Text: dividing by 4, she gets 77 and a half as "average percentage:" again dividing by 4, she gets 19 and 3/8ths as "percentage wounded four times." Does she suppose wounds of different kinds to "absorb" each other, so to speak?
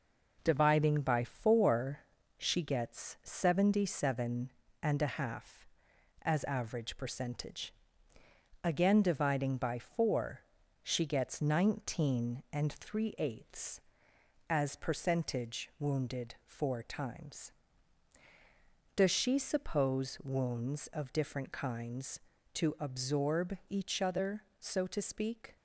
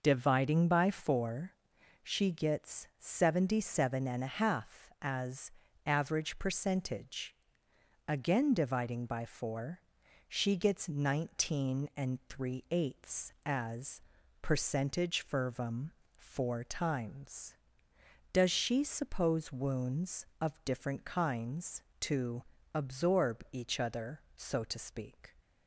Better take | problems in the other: first | pauses between "as" and "average"; slight; at 5.5 s; 0.34 s long // pauses between "as" and "percentage"; at 14.0 s; 0.40 s long // says "fervum" for "wounded"; at 15.2 s // pauses between "to" and "absorb"; slight; at 22.4 s; 0.28 s long

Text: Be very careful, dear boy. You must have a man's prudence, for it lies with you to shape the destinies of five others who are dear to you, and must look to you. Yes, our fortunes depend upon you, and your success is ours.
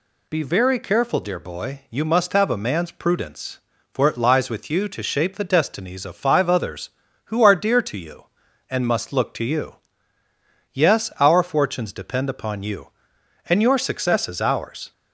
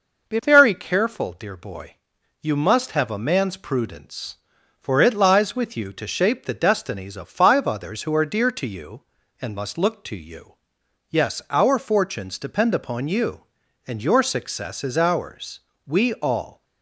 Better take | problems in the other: first | goes on to say "We all"; noticeable; from 15.8 s on; 0.78 s long

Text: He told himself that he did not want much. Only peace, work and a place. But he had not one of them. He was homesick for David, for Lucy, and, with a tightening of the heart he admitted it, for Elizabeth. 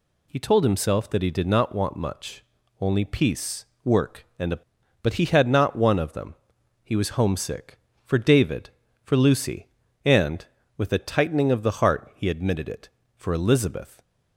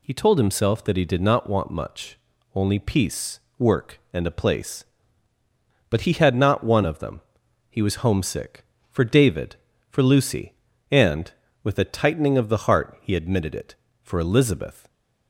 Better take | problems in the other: second | skips "place"; at 4.8 s

